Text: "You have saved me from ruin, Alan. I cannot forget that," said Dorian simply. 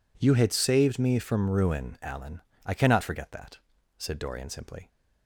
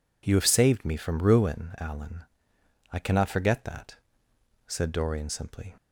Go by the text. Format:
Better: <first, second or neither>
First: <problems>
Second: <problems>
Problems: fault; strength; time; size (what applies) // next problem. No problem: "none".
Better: second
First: says "had" for "have"; at 0.3 s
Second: none